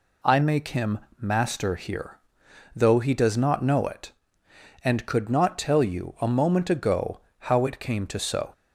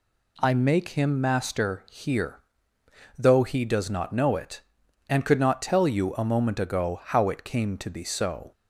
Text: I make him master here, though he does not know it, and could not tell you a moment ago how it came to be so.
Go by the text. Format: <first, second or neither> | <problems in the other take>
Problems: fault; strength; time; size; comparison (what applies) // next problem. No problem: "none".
second | pauses between "him" and "master"; slight; at 0.9 s; 0.20 s long // pauses between "ago" and "how"; slight; at 7.1 s; 0.20 s long // skips "be"; at 8.2 s